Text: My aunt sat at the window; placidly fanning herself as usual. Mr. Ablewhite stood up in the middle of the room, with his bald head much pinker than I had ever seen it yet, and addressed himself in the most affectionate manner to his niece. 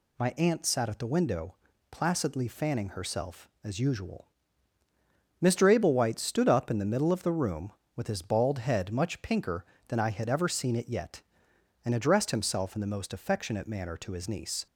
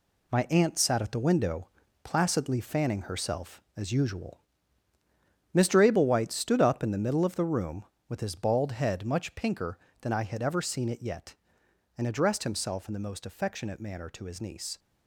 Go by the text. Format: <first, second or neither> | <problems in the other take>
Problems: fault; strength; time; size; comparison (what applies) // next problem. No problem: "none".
first | gets quieter; strong; throughout; 7.5 dB